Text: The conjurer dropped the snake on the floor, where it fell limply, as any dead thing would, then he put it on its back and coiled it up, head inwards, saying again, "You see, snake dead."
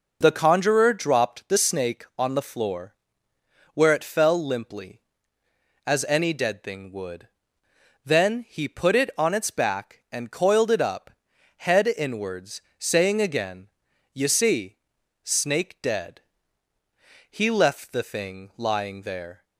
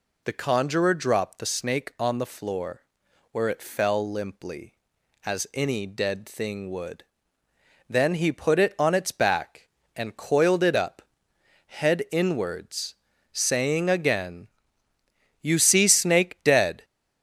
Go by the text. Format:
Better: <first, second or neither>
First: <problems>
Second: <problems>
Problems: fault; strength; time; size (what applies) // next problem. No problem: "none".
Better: second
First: goes on to say "He left the thing lying there"; strong; from 17.2 s on; 2.1 s long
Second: none